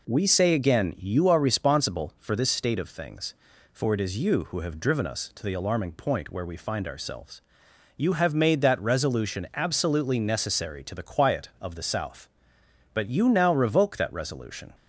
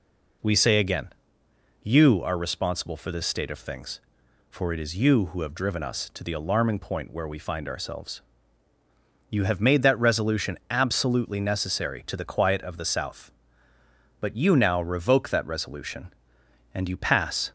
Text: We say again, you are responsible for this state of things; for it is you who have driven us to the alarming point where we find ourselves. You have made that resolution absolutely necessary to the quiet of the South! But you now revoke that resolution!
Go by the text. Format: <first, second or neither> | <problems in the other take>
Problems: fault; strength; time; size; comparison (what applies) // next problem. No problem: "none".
first | goes on to say "And you pass"; noticeable; from 16.7 s on; 0.78 s long